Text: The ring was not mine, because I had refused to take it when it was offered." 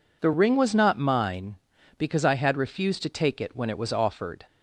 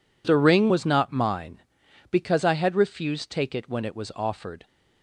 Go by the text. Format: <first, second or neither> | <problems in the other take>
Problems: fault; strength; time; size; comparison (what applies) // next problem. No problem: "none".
first | skips "to"; at 3.2 s